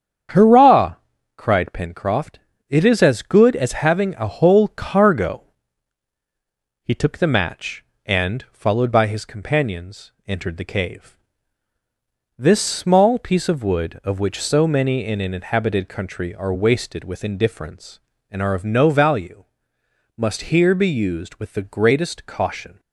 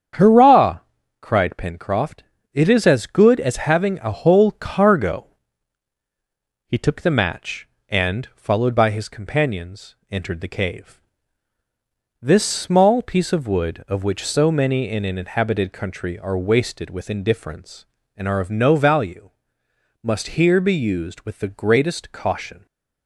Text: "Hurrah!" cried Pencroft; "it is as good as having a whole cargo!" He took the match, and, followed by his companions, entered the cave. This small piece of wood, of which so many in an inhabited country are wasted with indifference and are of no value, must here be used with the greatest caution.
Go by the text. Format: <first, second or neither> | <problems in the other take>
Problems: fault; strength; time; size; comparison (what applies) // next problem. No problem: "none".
neither | starts louder than the rest; strong; the same in both